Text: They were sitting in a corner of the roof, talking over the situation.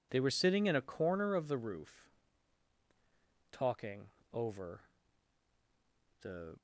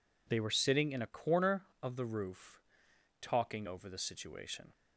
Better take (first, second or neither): second